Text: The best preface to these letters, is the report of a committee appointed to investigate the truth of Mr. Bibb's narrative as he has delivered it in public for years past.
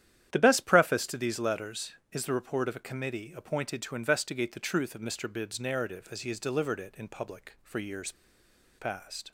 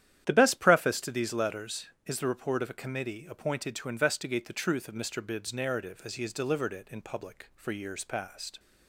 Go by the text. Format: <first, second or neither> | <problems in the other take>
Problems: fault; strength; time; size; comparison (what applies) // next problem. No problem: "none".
second | starts louder than the rest; strong; until 1.3 s; 10.5 dB; strong in the second // pauses between "years" and "past"; noticeable; at 8.1 s; 0.67 s long